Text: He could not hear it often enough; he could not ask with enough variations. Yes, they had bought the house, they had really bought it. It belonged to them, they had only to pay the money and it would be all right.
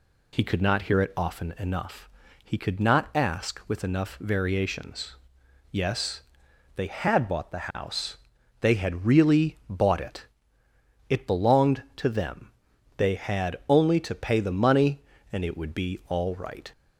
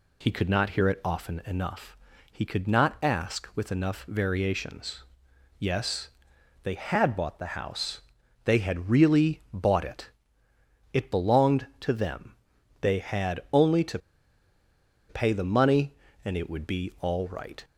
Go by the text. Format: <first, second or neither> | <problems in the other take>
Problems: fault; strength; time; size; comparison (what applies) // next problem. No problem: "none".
first | pauses between "to" and "pay"; at 13.9 s; 1.1 s long